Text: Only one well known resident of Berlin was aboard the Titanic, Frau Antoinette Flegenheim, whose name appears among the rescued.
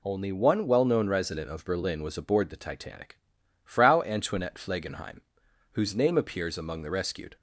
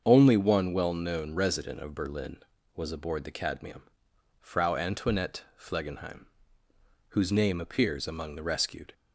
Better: first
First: none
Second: starts louder than the rest; until 1.0 s; 7 dB // says "Cadmium" for "Titanic"; at 3.3 s

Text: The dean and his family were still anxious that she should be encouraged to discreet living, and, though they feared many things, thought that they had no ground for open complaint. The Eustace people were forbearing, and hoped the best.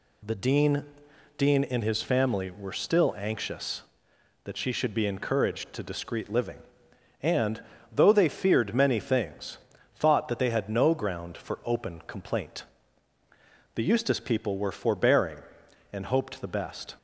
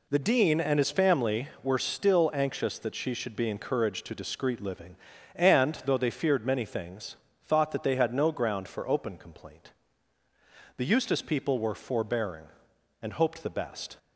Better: second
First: says "dean" twice; at 1.3 s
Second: none

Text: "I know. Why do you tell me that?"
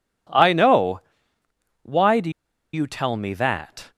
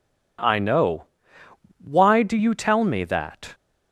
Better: second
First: pauses between "do" and "you"; at 2.2 s; 0.43 s long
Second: none

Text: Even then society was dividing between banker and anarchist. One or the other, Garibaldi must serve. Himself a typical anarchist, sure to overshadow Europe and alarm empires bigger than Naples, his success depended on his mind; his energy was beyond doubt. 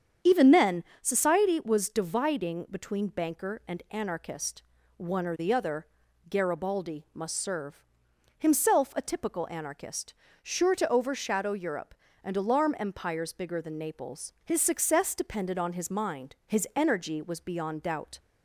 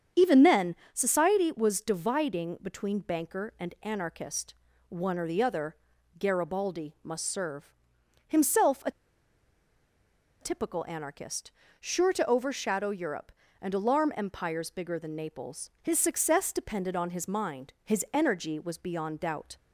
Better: first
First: starts louder than the rest; strong; until 1.4 s; 8 dB // pauses between "then" and "society"; slight; at 0.8 s; 0.18 s long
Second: starts louder than the rest; strong; until 1.3 s; 8 dB // pauses between "then" and "society"; slight; at 0.7 s; 0.18 s long // pauses between "a" and "typical"; strong; at 8.8 s; 1.5 s long

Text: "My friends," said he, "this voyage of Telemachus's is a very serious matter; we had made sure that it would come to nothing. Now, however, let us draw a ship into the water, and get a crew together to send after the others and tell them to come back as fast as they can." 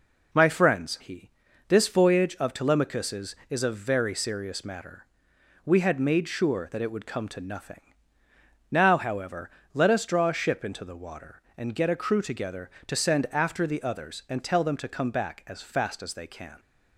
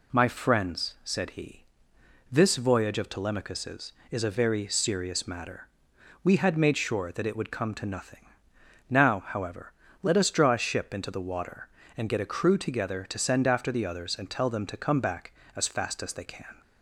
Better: second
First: skips "said"; at 0.9 s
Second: none

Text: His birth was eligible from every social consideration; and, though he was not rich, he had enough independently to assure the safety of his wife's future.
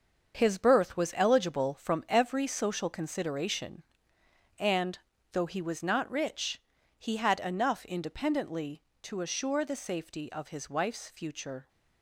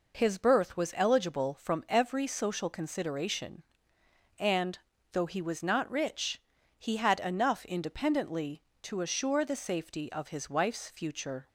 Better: second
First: gets quieter; strong; throughout; 8.5 dB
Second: none

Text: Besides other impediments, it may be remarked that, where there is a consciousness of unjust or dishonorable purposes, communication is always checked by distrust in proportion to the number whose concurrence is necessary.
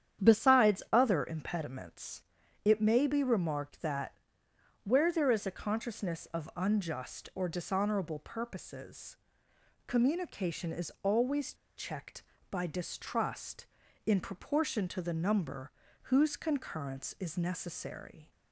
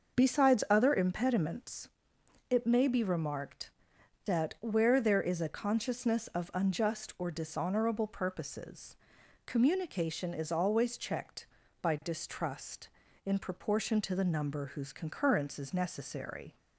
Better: second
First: starts louder than the rest; strong; until 1.3 s; 9.5 dB // pauses between "always" and "checked"; slight; at 11.5 s; 0.23 s long // pauses between "number" and "whose"; slight; at 15.7 s; 0.32 s long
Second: starts louder than the rest; until 1.2 s; 6 dB

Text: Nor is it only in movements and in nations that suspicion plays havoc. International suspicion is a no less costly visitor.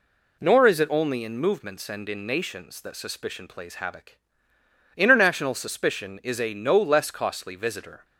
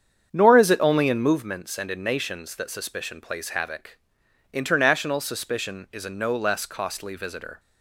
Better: first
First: none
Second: starts louder than the rest; strong; until 1.5 s; 8 dB

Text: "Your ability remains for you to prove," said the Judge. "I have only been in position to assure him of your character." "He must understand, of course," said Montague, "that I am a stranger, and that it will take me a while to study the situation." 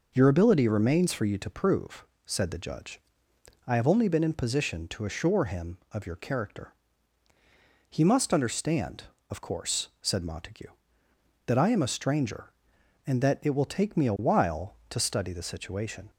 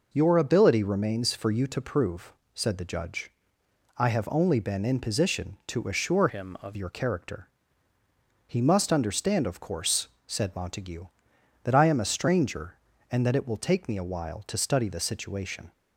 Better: first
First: none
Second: changes voice from "him" to "of"; from 6.2 to 6.7 s; 0.5 s long

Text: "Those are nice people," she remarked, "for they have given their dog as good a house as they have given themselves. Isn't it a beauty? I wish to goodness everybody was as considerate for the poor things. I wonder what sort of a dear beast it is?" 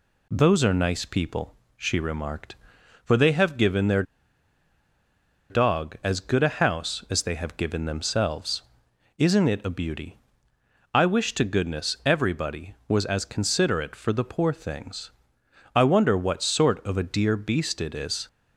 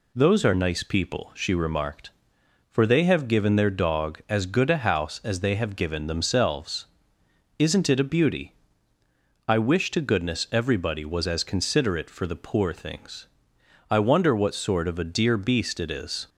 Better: second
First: pauses between "their" and "dog"; strong; at 4.0 s; 1.4 s long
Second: none

